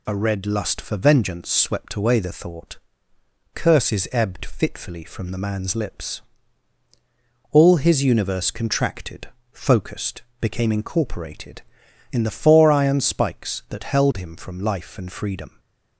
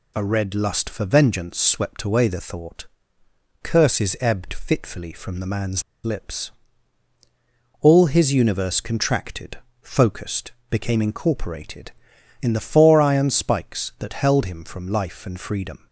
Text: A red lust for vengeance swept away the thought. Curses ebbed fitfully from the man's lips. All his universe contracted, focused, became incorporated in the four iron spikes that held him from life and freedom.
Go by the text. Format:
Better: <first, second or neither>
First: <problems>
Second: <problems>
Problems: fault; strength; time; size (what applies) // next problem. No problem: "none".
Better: first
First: none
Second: pauses between "man's" and "lips"; slight; at 5.8 s; 0.22 s long